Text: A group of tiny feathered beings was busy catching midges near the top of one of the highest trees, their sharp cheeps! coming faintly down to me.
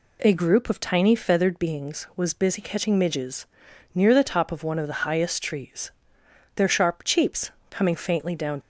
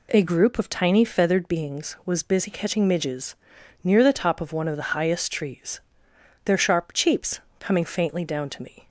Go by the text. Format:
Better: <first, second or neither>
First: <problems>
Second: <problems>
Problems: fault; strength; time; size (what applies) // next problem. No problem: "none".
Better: second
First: pauses between "midges" and "near"; noticeable; at 3.4 s; 0.48 s long // stops before "to me"; at 8.6 s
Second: pauses between "midges" and "near"; noticeable; at 3.3 s; 0.48 s long